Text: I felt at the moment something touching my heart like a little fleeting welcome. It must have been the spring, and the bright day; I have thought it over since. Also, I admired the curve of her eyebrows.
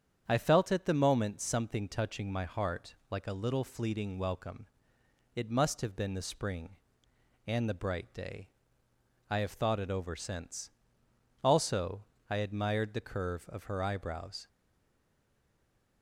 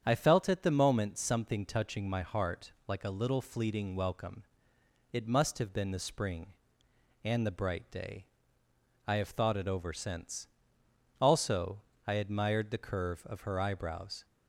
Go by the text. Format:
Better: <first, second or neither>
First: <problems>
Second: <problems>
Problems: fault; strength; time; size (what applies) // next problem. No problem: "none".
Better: second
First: starts louder than the rest; strong; until 1.2 s; 8.5 dB // pauses between "heart" and "like"; slight; at 2.9 s; 0.16 s long // stays silent after the last word; noticeable; from 14.4 s on; 1.6 s long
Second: starts louder than the rest; strong; until 1.0 s; 8.5 dB // pauses between "heart" and "like"; slight; at 2.7 s; 0.16 s long